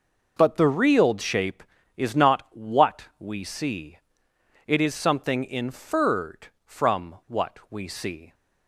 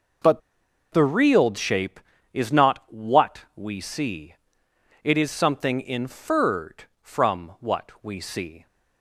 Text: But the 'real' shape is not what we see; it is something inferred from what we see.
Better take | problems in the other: first | pauses between "But" and "the"; noticeable; at 0.4 s; 0.51 s long

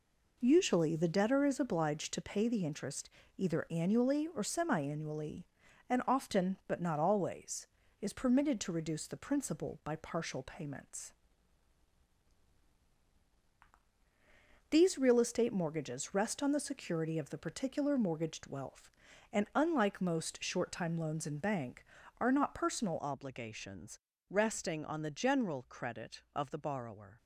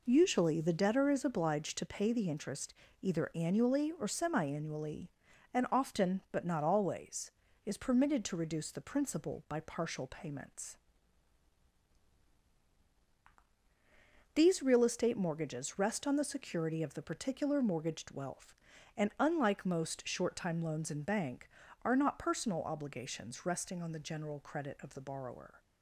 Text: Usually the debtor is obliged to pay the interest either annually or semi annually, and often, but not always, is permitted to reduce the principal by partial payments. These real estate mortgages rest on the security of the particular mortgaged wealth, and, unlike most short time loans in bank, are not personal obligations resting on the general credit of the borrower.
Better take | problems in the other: second | pauses between "interest" and "either"; slight; at 3.0 s; 0.28 s long; slight in the second // changes voice at "obligations"; from 22.9 s on; 4.2 s long // pauses between "obligations" and "resting"; slight; at 23.9 s; 0.32 s long

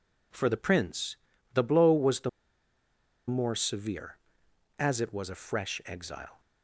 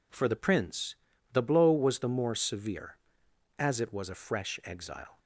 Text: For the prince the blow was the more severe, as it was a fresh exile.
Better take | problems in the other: second | pauses between "prince" and "the"; slight; at 1.1 s; 0.34 s long; slight in the second // pauses between "the" and "more"; at 2.2 s; 0.98 s long

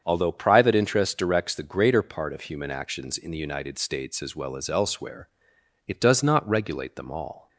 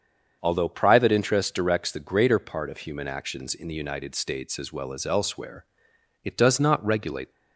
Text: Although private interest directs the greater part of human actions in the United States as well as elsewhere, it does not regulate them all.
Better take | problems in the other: first | starts louder than the rest; until 1.4 s; 7 dB; strong in the first // stops before "them all"; at 7.3 s

